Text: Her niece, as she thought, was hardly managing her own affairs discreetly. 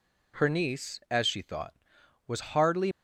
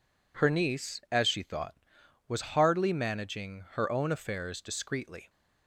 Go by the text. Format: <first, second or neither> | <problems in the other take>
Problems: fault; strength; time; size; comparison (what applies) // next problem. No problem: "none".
second | stops before "managing her own affairs discreetly"; at 2.9 s